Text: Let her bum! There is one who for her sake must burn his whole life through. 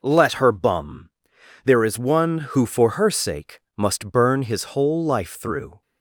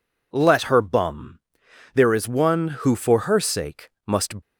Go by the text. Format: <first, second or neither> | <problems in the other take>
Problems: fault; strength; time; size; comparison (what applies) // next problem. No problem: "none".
first | pauses between "sake" and "must"; slight; at 3.8 s; 0.18 s long; slight in the first // stops before "burn his whole life through"; at 4.4 s